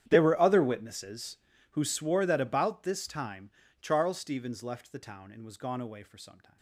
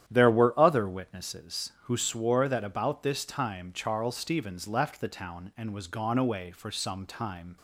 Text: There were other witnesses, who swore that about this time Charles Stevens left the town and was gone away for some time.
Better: second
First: gets quieter; strong; throughout; 21 dB // starts louder than the rest; strong; until 1.0 s; 10 dB // pauses between "time" and "Charles"; slight; at 3.5 s; 0.30 s long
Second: starts louder than the rest; strong; until 1.0 s; 10.5 dB

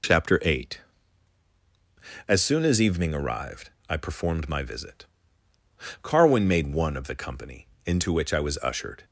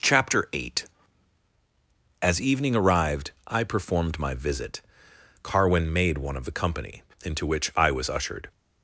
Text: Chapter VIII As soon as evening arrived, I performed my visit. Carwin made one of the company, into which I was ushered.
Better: first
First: none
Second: skips "As soon"; at 1.5 s

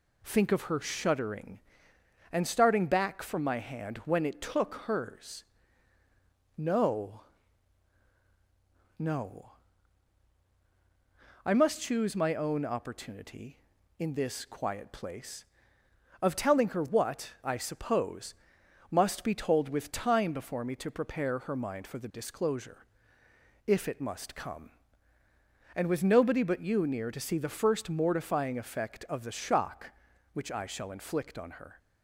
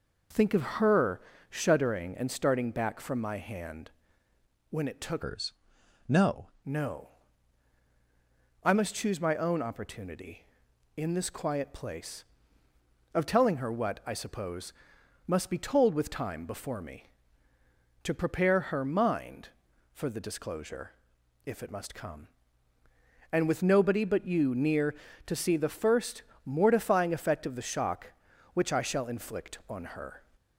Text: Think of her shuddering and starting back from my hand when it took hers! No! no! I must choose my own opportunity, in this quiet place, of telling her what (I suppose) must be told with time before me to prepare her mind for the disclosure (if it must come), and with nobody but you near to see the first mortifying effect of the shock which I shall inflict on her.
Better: first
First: none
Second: pauses between "her" and "shuddering"; slight; at 1.1 s; 0.30 s long // pauses between "hand" and "when"; noticeable; at 3.9 s; 0.78 s long // changes voice from "hers" to "No"; from 5.2 to 6.5 s; 1.3 s long // pauses between "first" and "mortifying"; slight; at 26.2 s; 0.20 s long

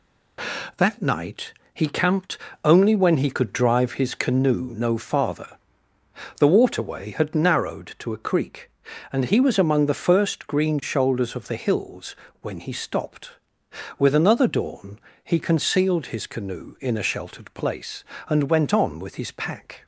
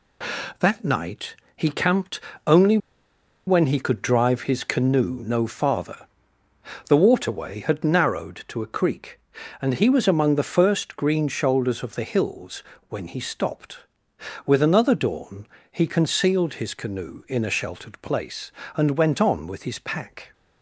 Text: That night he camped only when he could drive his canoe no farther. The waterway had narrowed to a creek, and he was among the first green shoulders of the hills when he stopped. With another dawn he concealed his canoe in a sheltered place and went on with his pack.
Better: first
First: pauses between "night" and "he"; slight; at 1.5 s; 0.20 s long // pauses between "camped" and "only"; slight; at 2.3 s; 0.26 s long // pauses between "hills" and "when"; slight; at 12.1 s; 0.26 s long // pauses between "dawn" and "he"; slight; at 14.9 s; 0.24 s long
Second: pauses between "night" and "he"; slight; at 1.3 s; 0.20 s long // pauses between "camped" and "only"; slight; at 2.1 s; 0.26 s long // pauses between "only" and "when"; noticeable; at 2.7 s; 0.69 s long // pauses between "hills" and "when"; slight; at 12.6 s; 0.26 s long // pauses between "dawn" and "he"; slight; at 15.4 s; 0.24 s long

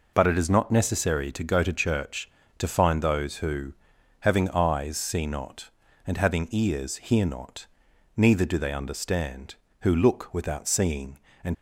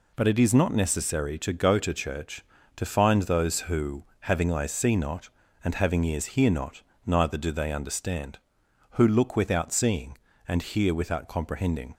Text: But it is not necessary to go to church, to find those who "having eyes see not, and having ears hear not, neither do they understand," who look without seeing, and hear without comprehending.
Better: second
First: pauses between "who" and "having"; noticeable; at 3.7 s; 0.48 s long // stops before "hear without comprehending"; at 11.5 s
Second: pauses between "who" and "having"; slight; at 4.0 s; 0.18 s long

